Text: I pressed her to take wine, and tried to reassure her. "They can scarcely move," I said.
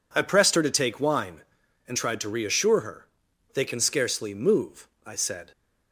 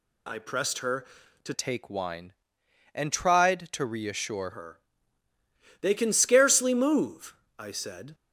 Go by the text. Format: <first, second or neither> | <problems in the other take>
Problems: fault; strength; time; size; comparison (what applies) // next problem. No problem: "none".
first | changes voice from "take" to "reassure"; from 1.5 to 4.4 s; 2.9 s long